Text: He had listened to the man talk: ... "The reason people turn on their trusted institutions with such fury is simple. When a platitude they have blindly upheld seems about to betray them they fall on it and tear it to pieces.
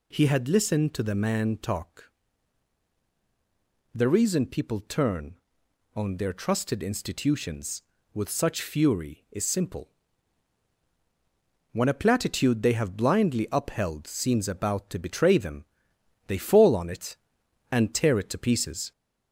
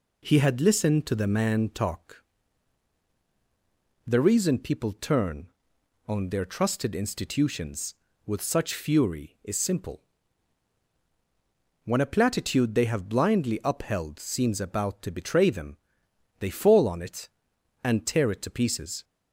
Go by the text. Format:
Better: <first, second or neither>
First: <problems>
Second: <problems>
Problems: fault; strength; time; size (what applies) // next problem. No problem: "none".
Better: second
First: gets louder; slight; throughout; 2 dB // pauses between "them" and "they"; noticeable; at 15.6 s; 0.64 s long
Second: pauses between "them" and "they"; noticeable; at 15.7 s; 0.64 s long